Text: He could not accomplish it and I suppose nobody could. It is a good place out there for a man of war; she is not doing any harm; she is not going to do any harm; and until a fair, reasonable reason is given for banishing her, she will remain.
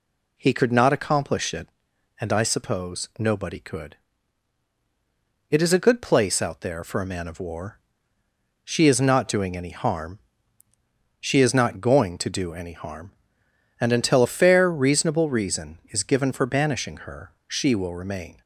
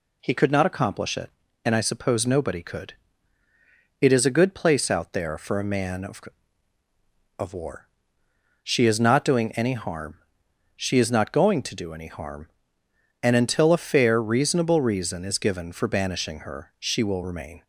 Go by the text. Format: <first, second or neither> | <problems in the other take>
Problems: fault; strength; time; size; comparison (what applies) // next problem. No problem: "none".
first | says "of" twice; at 7.3 s